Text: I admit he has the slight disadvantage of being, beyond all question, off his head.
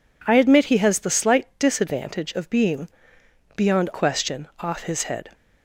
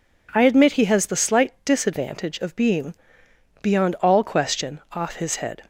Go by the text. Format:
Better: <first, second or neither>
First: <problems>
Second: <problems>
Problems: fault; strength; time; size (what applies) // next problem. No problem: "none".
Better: second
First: skips "all"; at 3.9 s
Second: none